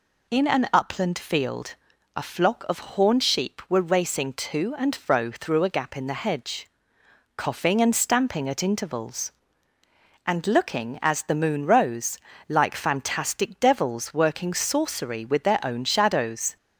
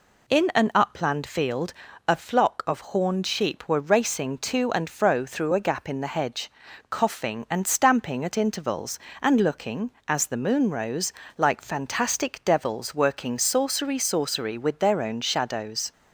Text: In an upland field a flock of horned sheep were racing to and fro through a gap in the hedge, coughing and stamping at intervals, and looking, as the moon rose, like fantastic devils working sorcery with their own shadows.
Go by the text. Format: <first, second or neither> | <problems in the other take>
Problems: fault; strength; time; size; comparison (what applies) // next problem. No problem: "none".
first | pauses between "field" and "a"; slight; at 1.7 s; 0.36 s long; also in the first // says "sorcery" twice; at 13.9 s